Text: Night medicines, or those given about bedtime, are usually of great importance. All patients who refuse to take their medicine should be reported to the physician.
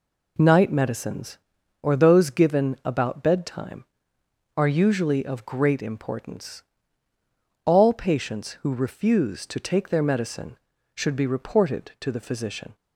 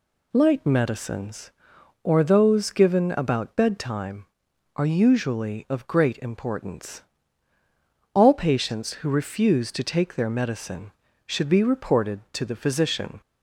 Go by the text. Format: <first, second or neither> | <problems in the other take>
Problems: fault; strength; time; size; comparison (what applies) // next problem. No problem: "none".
first | says "Light" for "Night"; at 0.3 s